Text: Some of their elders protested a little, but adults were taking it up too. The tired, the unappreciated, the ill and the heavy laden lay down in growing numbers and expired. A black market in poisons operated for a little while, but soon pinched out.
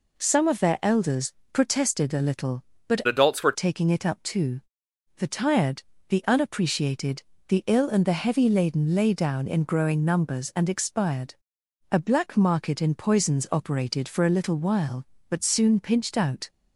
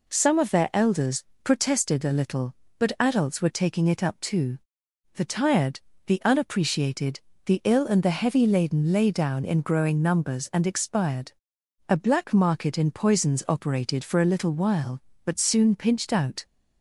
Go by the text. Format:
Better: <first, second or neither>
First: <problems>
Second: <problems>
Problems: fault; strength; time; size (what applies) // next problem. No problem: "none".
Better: second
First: pauses between "elders" and "protested"; slight; at 1.3 s; 0.18 s long // changes voice from "adults" to "were"; from 3.0 to 3.5 s; 0.5 s long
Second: pauses between "elders" and "protested"; slight; at 1.2 s; 0.18 s long